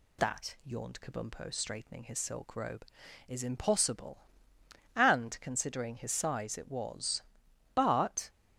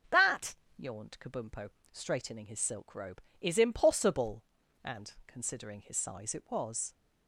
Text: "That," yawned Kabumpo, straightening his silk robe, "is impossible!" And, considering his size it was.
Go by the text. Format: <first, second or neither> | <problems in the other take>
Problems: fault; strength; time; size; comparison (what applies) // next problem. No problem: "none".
second | goes on to say "But"; from 7.7 s on; 0.56 s long